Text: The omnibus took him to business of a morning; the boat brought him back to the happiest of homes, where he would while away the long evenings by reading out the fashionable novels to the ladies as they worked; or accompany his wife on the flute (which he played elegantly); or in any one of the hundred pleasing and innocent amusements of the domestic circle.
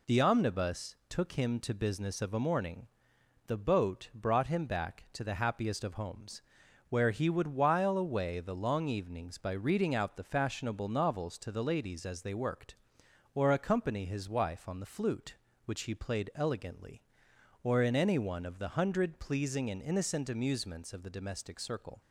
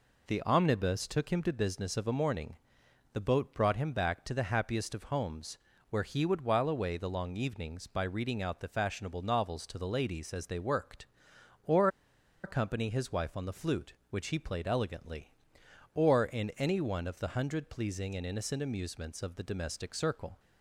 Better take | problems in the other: first | pauses between "or" and "accompany"; noticeable; at 11.8 s; 0.55 s long

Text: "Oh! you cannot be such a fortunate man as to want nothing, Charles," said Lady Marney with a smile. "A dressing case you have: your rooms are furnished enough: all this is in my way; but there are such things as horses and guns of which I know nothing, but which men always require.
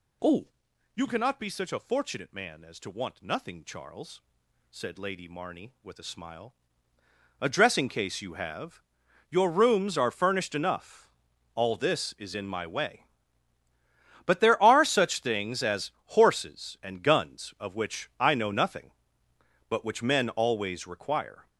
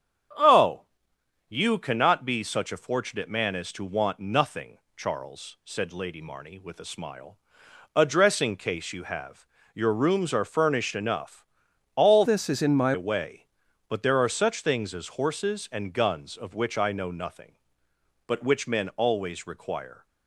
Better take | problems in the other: first | starts louder than the rest; strong; until 2.0 s; 8 dB // changes voice from "this" to "my"; from 12.2 to 12.9 s; 0.7 s long

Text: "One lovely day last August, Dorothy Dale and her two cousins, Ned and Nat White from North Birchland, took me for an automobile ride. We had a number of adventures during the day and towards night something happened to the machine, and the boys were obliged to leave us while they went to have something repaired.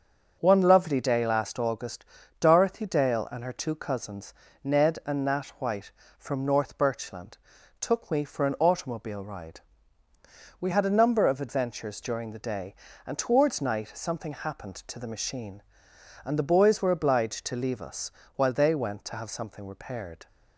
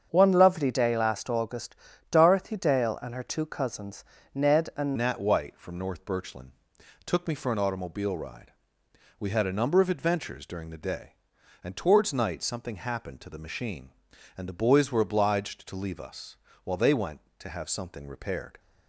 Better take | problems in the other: first | starts louder than the rest; strong; until 1.1 s; 7.5 dB // changes voice at "Nat"; from 4.9 s on; 13.6 s long // pauses between "us" and "while"; slight; at 16.3 s; 0.26 s long; slight in the first

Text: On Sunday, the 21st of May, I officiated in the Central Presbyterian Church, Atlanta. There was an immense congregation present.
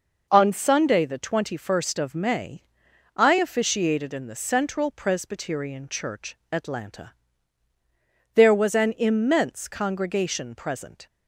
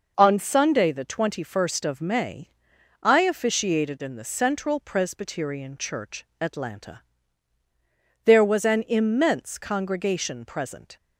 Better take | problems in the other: neither | none

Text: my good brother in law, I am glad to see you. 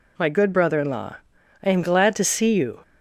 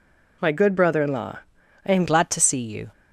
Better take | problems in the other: first | changes voice at "glad"; from 2.0 s on; 0.9 s long

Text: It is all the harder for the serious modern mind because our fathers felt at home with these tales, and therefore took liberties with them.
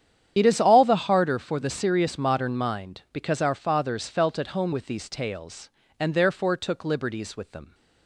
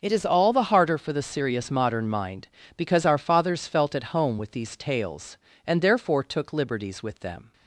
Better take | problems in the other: second | loses the start of "It"; at 0.3 s; 30 ms // starts louder than the rest; strong; until 1.3 s; 9.5 dB

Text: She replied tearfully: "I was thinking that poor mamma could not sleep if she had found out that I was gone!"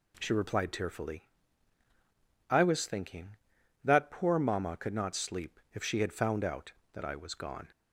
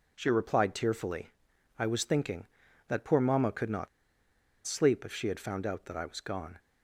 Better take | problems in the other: first | pauses between "not" and "sleep"; noticeable; at 3.8 s; 0.78 s long

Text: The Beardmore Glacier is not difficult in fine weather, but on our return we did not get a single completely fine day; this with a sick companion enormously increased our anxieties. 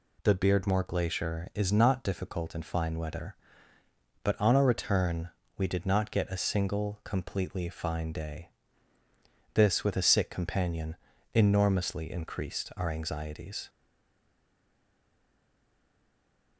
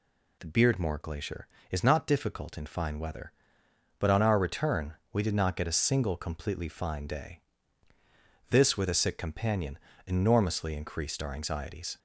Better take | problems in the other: second | pauses between "return" and "we"; slight; at 5.2 s; 0.26 s long; slight in the second // pauses between "companion" and "enormously"; slight; at 10.9 s; 0.36 s long; slight in the second // stays silent after the last word; strong; from 13.6 s on; 2.9 s long

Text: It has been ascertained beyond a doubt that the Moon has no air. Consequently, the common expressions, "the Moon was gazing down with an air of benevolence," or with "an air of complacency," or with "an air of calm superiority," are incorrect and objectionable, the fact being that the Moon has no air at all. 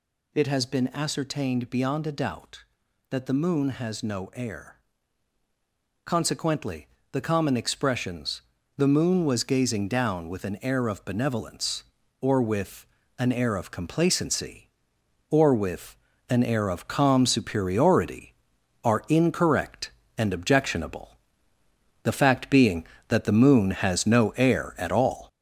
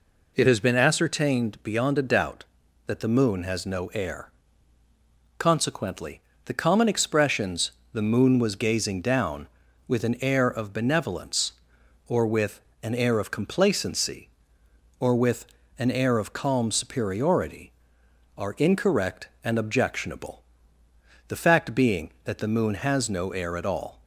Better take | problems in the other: second | gets louder; noticeable; throughout; 5.5 dB // pauses between "with" and "an"; slight; at 12.8 s; 0.32 s long; slight in the second // pauses between "with" and "an"; slight; at 15.9 s; 0.32 s long; slight in the second

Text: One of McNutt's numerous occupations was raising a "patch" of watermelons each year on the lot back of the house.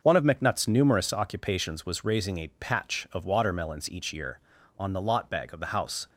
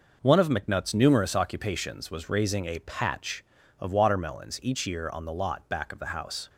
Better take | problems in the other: second | starts louder than the rest; until 1.0 s; 6.5 dB // says "bag" for "back"; at 5.2 s

